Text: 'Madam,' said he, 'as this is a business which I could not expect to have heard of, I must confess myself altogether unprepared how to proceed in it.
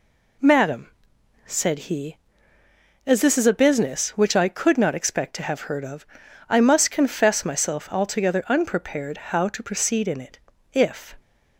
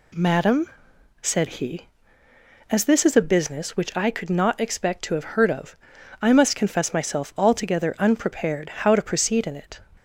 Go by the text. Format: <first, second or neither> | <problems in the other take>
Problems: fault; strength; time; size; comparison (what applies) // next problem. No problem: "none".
second | goes on to say "If"; slight; from 10.7 s on; 0.44 s long